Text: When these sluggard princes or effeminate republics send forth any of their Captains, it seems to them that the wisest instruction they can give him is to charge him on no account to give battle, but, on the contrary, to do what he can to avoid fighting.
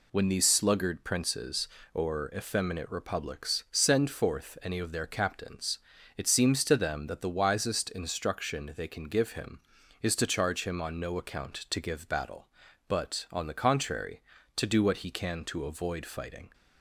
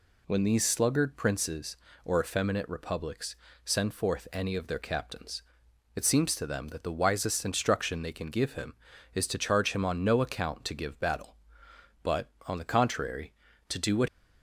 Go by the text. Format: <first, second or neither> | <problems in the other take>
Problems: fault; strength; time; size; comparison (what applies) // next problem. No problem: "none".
first | pauses between "republics" and "send"; slight; at 3.3 s; 0.26 s long // stops before "he can to avoid fighting"; at 14.0 s